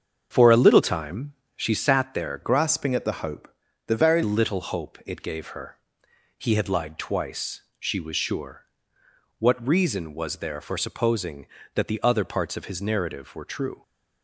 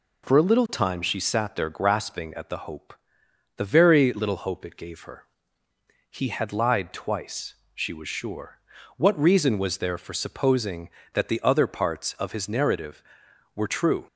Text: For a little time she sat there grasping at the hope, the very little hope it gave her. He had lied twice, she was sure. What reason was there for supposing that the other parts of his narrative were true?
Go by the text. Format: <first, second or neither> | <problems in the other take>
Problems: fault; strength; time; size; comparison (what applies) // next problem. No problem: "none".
second | starts louder than the rest; strong; until 1.3 s; 7 dB // pauses between "time" and "she"; slight; at 1.3 s; 0.24 s long // changes voice from "grasping" to "very"; from 2.4 to 4.2 s; 1.8 s long